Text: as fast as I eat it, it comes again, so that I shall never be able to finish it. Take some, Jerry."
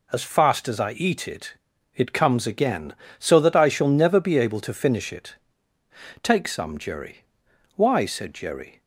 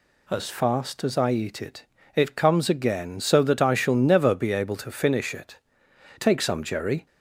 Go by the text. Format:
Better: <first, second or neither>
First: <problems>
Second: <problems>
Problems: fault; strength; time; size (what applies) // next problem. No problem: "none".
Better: second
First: goes on to say "Why said Jerry"; noticeable; from 7.7 s on; 1.0 s long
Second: none